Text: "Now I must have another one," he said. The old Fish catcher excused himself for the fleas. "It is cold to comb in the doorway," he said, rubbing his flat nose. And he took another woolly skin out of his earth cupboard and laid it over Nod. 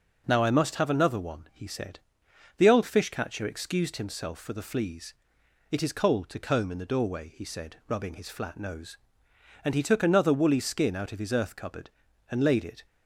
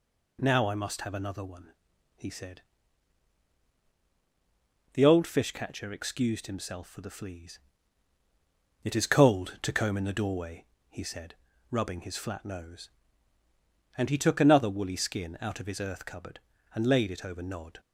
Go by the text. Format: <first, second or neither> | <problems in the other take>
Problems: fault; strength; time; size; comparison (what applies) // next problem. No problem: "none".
second | stops before "over Nod"; at 12.8 s